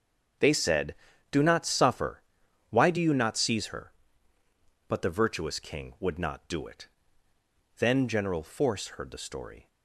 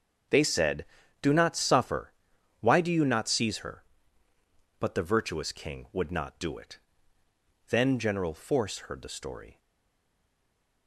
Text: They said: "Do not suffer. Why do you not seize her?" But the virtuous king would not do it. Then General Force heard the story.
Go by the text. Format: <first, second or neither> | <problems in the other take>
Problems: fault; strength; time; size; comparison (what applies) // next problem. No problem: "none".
first | starts louder than the rest; until 1.6 s; 6.5 dB; also in the first // stays silent after the last word; noticeable; from 9.5 s on; 1.3 s long